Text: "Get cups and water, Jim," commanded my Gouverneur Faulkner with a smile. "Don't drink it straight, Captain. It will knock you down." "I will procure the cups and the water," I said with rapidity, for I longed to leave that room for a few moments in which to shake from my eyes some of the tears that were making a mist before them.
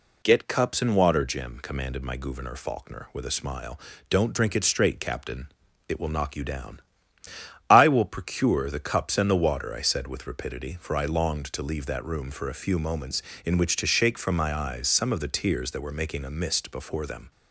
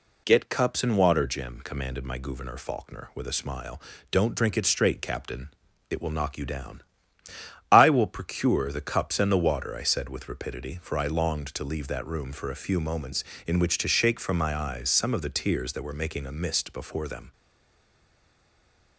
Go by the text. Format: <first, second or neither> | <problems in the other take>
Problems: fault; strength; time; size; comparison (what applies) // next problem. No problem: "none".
first | stays silent after the last word; noticeable; from 17.3 s on; 1.6 s long